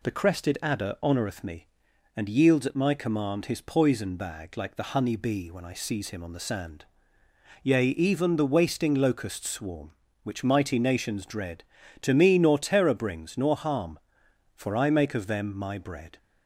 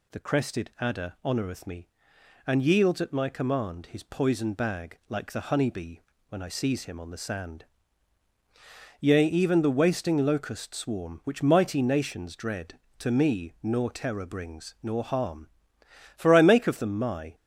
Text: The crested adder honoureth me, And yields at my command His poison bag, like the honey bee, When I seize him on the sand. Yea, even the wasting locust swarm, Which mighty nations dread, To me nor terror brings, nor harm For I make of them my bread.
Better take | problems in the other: first | stops before "bread"; at 17.3 s

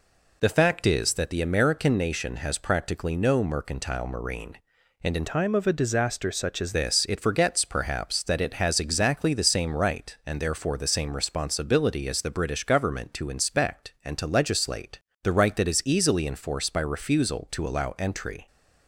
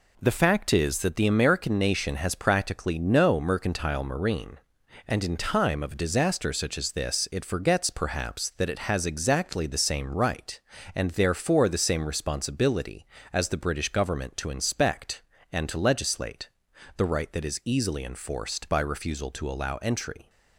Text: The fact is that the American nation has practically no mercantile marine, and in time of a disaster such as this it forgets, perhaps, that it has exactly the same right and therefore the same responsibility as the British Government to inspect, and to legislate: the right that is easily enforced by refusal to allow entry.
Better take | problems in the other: second | changes voice from "time" to "as"; from 5.2 to 6.7 s; 1.5 s long

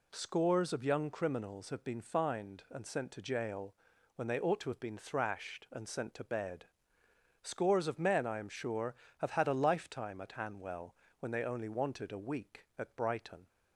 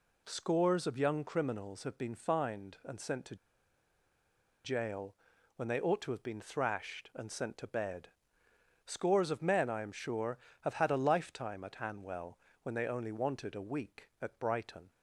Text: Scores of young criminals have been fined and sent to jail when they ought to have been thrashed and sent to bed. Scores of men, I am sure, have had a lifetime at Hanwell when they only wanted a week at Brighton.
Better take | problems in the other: first | pauses between "to" and "jail"; strong; at 3.3 s; 1.2 s long // pauses between "jail" and "when"; at 5.1 s; 0.40 s long; also in the first // pauses between "Hanwell" and "when"; slight; at 12.3 s; 0.24 s long; slight in the first

